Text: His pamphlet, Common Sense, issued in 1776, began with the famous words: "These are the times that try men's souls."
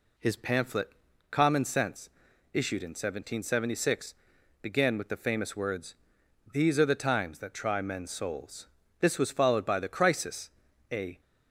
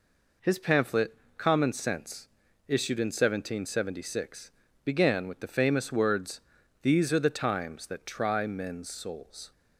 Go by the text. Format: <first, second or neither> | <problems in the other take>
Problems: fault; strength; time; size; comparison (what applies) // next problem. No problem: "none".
second | goes on to say "This was followed by the Crisis a"; strong; from 8.9 s on; 2.2 s long